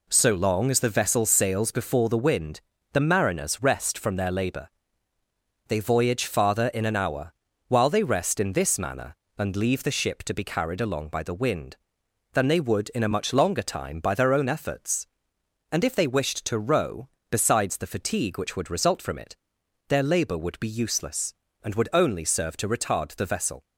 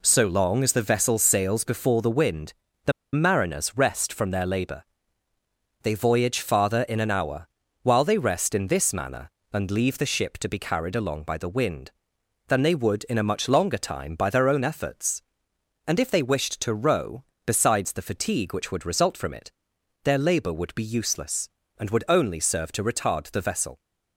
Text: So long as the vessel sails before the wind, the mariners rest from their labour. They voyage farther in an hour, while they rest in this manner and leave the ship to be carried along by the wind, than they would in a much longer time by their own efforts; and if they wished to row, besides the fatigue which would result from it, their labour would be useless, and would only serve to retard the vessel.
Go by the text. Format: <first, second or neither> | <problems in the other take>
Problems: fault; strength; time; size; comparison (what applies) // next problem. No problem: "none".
first | pauses between "the" and "mariners"; slight; at 2.9 s; 0.21 s long